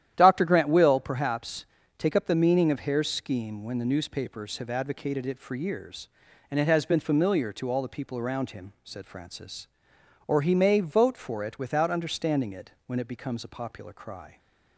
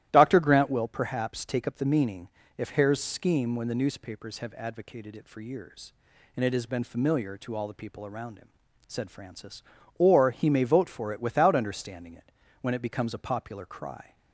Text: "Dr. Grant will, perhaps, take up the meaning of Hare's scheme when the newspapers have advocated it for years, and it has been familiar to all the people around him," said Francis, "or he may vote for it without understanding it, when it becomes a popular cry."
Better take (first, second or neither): first